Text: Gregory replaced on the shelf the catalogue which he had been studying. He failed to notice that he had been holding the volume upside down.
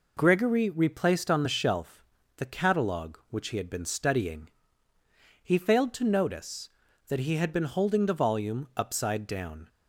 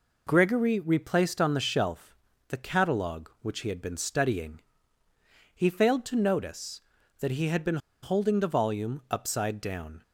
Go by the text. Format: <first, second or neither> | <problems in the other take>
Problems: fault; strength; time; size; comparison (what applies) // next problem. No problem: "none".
first | pauses between "shelf" and "the"; slight; at 2.1 s; 0.36 s long; slight in the first // pauses between "been" and "holding"; slight; at 7.7 s; 0.24 s long